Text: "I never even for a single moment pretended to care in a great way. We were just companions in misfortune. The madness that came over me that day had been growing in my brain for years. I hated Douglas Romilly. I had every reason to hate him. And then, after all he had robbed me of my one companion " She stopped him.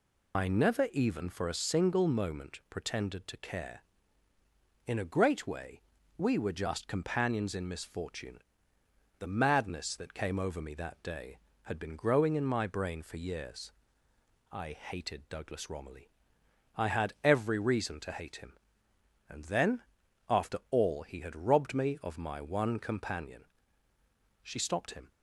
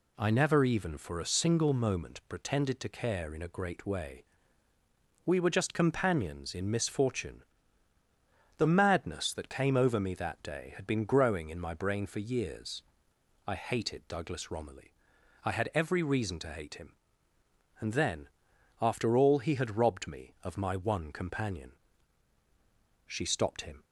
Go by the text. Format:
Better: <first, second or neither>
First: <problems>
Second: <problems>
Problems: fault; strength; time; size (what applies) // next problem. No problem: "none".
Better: second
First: loses the start of "I"; at 0.3 s; 120 ms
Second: none